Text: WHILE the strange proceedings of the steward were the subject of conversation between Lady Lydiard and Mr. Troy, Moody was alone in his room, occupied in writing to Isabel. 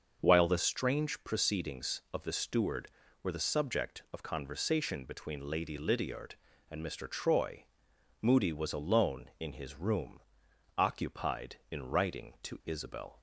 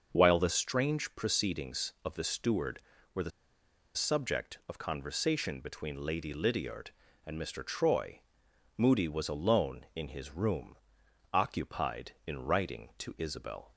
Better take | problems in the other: first | starts louder than the rest; until 1.1 s; 6.5 dB; also in the first // pauses between "the" and "subject"; noticeable; at 3.3 s; 0.65 s long

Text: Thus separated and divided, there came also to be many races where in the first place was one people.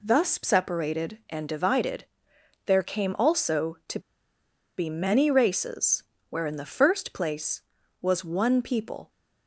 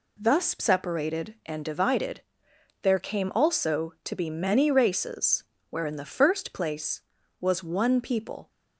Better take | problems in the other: second | pauses between "to" and "be"; noticeable; at 3.9 s; 0.78 s long // pauses between "races" and "where"; slight; at 6.0 s; 0.26 s long; slight in the second

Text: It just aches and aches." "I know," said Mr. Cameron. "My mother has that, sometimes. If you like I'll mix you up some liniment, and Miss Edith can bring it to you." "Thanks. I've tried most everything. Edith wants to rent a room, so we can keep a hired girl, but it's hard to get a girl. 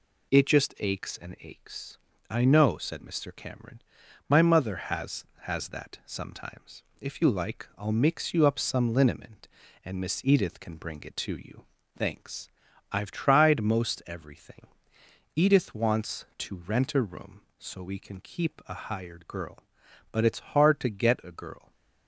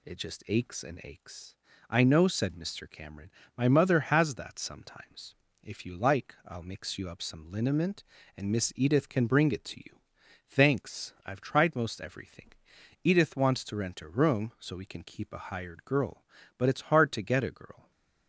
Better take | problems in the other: second | says "has" twice; at 5.4 s

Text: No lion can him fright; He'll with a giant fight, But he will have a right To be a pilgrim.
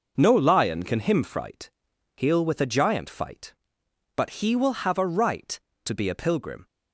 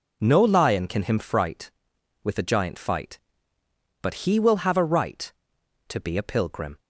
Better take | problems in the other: first | skips "He'll"; at 1.9 s

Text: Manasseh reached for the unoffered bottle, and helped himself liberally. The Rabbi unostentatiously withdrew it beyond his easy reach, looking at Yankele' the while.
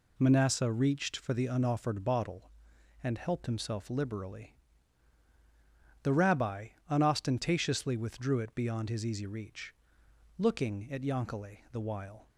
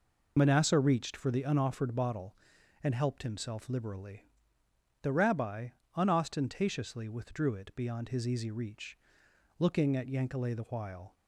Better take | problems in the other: first | loses the start of "Manasseh"; at 0.3 s; 70 ms // pauses between "Rabbi" and "unostentatiously"; slight; at 5.6 s; 0.26 s long; slight in the first

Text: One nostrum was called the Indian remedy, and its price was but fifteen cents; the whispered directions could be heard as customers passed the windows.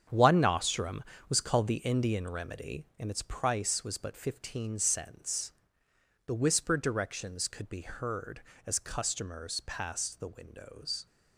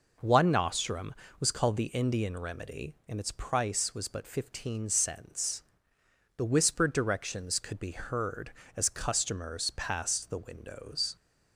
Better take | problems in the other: second | gets quieter; strong; throughout; 9.5 dB

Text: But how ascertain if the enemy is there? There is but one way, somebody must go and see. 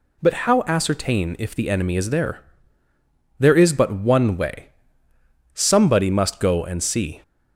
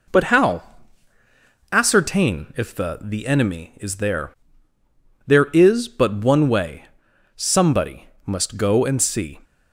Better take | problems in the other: first | pauses between "how" and "ascertain"; at 0.6 s; 1.0 s long // says "the" twice; at 3.0 s // pauses between "somebody" and "must"; slight; at 8.0 s; 0.16 s long

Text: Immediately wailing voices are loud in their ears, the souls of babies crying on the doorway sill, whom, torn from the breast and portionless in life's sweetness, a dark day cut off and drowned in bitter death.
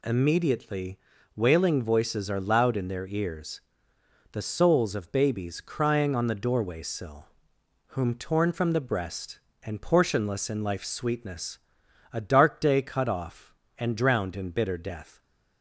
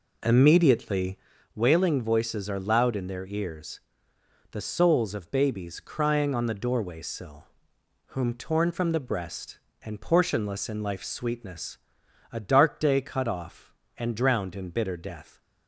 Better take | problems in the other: first | starts louder than the rest; until 1.4 s; 4 dB // pauses between "Immediately" and "wailing"; at 1.1 s; 0.38 s long; also in the first

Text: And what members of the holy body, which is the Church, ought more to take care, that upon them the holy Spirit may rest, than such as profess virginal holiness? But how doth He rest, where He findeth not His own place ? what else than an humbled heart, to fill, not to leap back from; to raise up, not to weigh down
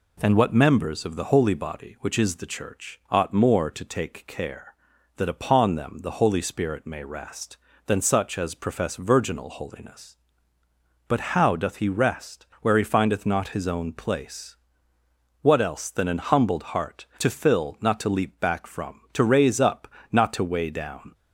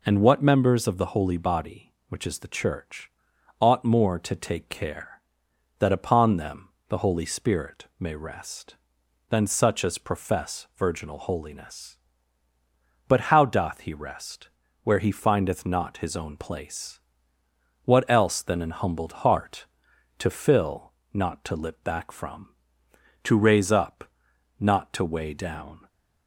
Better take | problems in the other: first | pauses between "them" and "the"; slight; at 6.6 s; 0.18 s long // says "lip" for "leap"; at 21.5 s

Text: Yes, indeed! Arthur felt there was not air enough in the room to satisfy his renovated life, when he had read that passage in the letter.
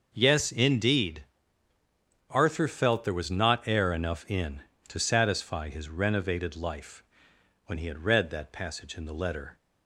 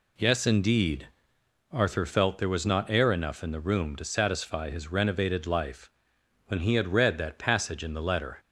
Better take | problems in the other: second | starts louder than the rest; noticeable; until 1.1 s; 6 dB // skips "the room"; at 4.7 s

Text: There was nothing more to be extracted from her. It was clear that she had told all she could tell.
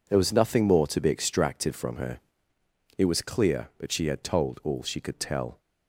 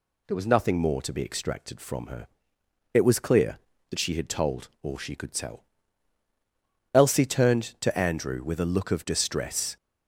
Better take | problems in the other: first | goes on to say "Elsie turned to Andrew with a look of distress"; strong; from 6.9 s on; 2.8 s long

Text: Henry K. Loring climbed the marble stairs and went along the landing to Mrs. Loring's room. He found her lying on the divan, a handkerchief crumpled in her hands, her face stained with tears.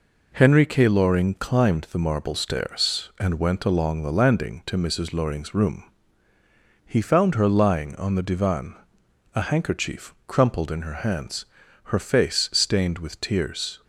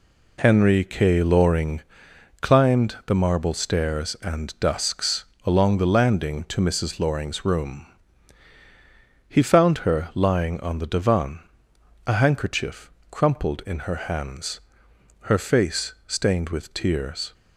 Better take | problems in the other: first | pauses between "Loring" and "climbed"; noticeable; at 1.8 s; 0.58 s long // says "dusks" for "went"; at 4.6 s // pauses between "handkerchief" and "crumpled"; slight; at 12.8 s; 0.22 s long

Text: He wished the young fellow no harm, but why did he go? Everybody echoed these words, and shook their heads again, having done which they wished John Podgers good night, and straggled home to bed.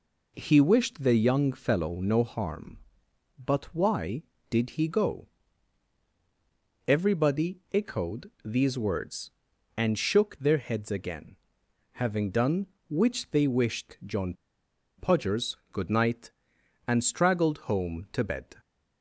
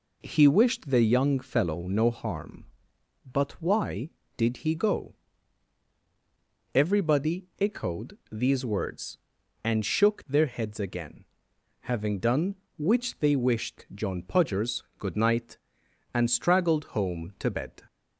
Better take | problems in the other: second | pauses between "John" and "Podgers"; noticeable; at 14.3 s; 0.65 s long

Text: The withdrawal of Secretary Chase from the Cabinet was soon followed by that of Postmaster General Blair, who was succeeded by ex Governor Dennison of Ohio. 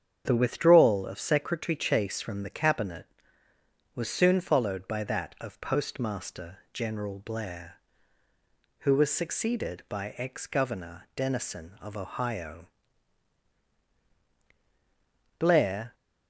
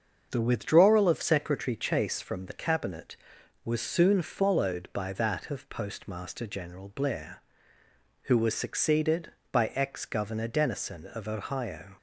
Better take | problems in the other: second | starts louder than the rest; strong; until 1.2 s; 8 dB; also in the second // goes on to say "Blair"; from 15.3 s on; 0.56 s long

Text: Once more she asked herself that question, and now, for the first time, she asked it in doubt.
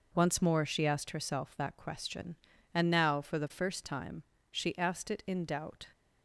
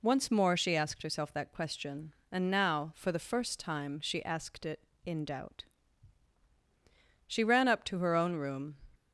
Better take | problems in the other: first | goes on to say "She ran up to her own room"; from 7.2 s on; 1.5 s long

